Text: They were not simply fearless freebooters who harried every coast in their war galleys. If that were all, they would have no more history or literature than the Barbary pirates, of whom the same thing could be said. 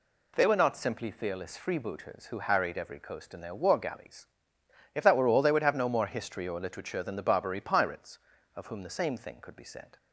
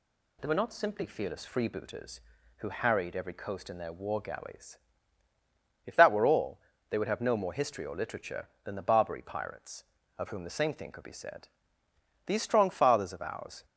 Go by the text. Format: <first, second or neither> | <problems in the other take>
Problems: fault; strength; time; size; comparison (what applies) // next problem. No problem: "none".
first | goes on to say "These strong fathers of ours"; from 12.2 s on; 1.3 s long